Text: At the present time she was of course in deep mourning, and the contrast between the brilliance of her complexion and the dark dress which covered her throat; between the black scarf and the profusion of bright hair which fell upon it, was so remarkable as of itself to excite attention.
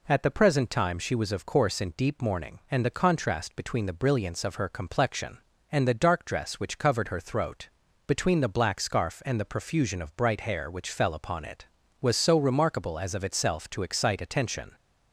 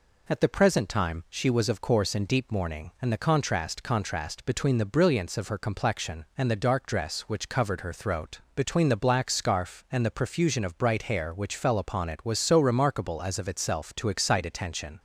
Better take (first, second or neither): first